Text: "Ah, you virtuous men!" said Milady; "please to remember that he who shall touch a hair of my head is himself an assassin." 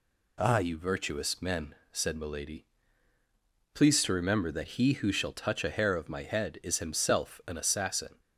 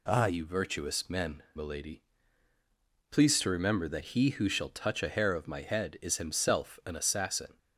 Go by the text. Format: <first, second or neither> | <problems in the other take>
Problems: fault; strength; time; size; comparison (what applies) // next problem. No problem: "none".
first | skips "said"; at 1.4 s